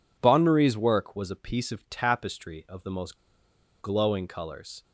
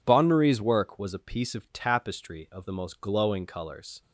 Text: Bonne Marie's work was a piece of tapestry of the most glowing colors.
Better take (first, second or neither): second